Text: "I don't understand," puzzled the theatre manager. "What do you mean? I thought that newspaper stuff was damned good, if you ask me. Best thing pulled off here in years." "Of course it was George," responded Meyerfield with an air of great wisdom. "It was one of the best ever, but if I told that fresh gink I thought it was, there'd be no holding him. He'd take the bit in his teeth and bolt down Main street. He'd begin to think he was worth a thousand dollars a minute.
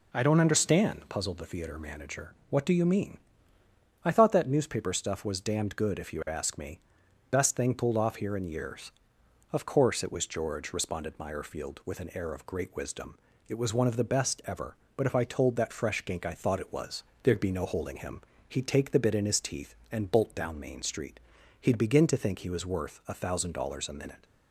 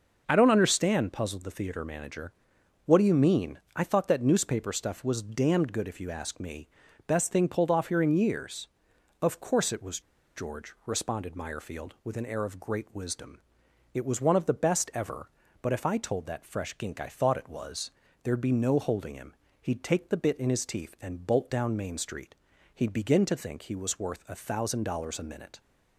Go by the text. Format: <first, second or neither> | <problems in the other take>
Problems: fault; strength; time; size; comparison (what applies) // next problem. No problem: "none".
first | pauses between "was" and "George"; slight; at 10.0 s; 0.35 s long